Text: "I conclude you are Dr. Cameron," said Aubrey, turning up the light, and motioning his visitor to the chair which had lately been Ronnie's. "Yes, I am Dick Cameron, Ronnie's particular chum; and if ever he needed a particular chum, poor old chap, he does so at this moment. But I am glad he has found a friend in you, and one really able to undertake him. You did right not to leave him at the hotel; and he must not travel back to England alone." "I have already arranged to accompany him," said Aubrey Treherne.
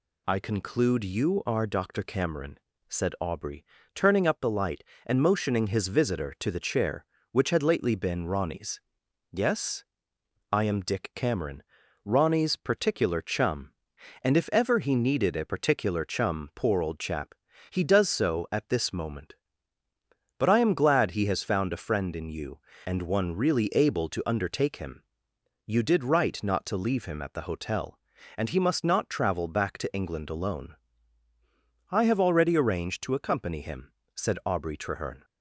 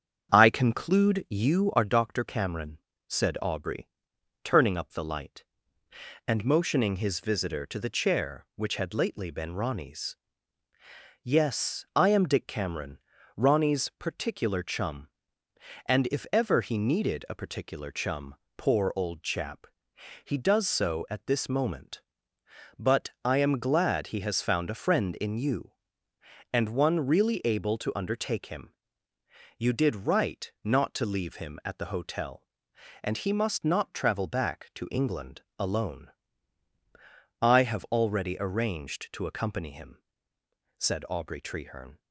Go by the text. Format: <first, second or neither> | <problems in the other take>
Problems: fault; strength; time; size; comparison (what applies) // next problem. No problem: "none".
first | starts louder than the rest; strong; until 2.0 s; 8 dB // pauses between "But" and "I"; slight; at 23.0 s; 0.16 s long // pauses between "England" and "alone"; slight; at 35.4 s; 0.16 s long